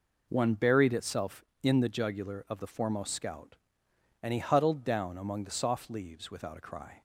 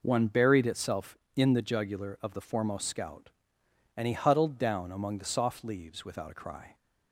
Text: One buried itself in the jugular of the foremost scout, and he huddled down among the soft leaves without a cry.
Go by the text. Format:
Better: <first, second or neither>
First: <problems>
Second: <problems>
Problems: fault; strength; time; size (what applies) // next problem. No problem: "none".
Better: neither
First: none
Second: none